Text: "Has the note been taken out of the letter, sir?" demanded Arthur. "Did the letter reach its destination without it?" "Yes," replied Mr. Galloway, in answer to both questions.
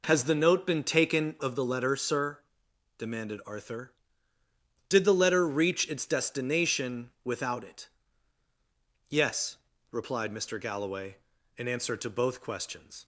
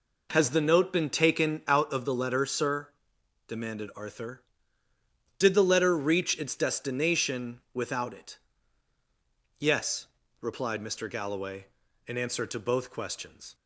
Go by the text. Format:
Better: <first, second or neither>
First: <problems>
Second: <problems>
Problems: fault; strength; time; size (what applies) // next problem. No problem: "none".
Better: second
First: skips "out"; at 1.3 s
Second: none